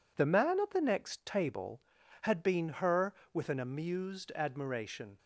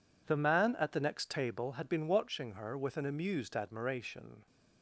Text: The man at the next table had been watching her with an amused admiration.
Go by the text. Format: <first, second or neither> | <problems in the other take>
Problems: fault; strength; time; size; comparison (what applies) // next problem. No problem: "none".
second | skips "watching"; at 2.6 s